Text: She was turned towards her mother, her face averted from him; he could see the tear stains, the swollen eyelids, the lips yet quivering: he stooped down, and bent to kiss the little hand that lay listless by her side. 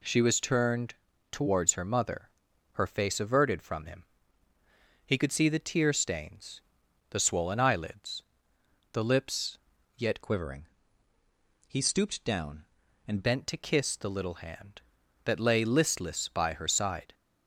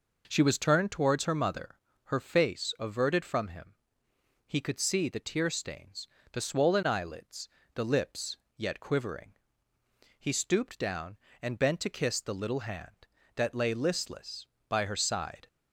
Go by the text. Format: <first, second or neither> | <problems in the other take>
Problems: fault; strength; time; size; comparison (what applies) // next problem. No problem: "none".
second | pauses between "turned" and "towards"; slight; at 0.9 s; 0.36 s long // pauses between "lips" and "yet"; at 9.5 s; 0.38 s long; slight in the second // changes voice from "quivering" to "and"; from 10.2 to 13.2 s; 3.0 s long